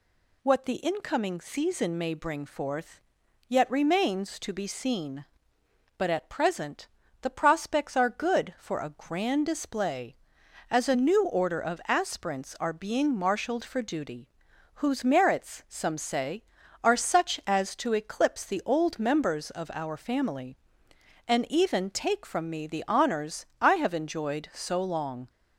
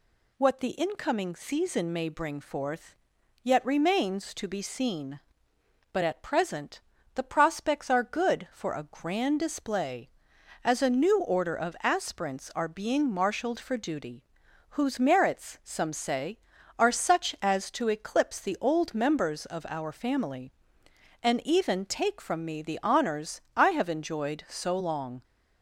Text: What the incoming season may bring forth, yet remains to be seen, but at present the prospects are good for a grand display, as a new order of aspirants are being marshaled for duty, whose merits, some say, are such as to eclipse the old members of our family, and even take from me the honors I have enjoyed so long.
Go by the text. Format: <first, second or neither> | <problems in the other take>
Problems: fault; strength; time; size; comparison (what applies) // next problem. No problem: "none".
neither | pauses between "present" and "the"; slight; the same in both